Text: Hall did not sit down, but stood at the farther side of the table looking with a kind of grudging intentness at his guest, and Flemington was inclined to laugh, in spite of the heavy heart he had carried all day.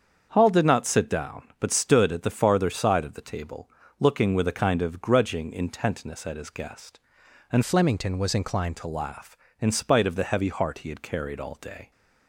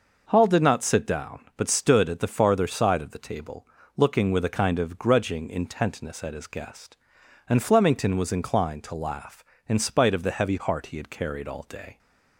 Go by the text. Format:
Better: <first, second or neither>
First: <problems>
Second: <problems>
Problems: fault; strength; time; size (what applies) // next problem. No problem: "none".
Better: second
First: starts louder than the rest; until 1.3 s; 7 dB // pauses between "table" and "looking"; slight; at 3.7 s; 0.30 s long // changes voice from "Flemington" to "inclined"; from 7.6 to 8.7 s; 1.1 s long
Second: pauses between "table" and "looking"; slight; at 3.6 s; 0.30 s long